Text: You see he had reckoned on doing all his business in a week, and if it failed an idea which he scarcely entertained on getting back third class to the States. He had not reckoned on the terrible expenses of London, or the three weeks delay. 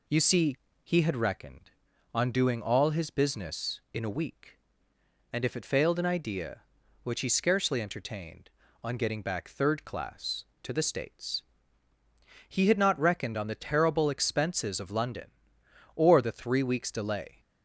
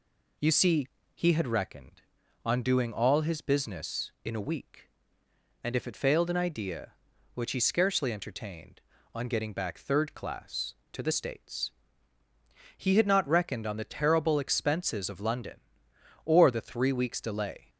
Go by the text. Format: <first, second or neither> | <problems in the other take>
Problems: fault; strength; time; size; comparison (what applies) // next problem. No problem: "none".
neither | pauses between "see" and "he"; slight; the same in both